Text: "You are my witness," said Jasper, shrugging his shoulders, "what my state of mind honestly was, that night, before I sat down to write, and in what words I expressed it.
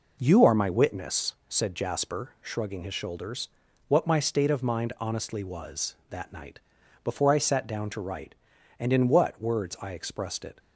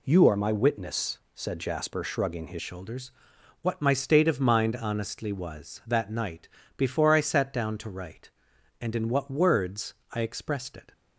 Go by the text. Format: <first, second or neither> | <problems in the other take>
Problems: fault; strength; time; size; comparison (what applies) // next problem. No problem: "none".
first | changes voice at "shoulders"; from 2.6 s on; 8.3 s long // pauses between "words" and "I"; slight; at 9.9 s; 0.18 s long